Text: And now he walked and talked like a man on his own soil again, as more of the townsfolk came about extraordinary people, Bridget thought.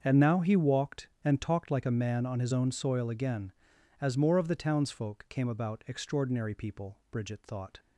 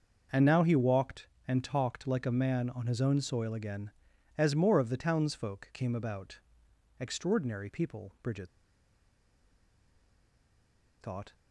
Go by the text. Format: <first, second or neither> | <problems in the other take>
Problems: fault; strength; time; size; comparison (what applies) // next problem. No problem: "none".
first | starts louder than the rest; until 1.5 s; 6 dB; also in the first // pauses between "about" and "extraordinary"; noticeable; at 6.3 s; 0.62 s long // pauses between "Bridget" and "thought"; strong; at 8.4 s; 2.5 s long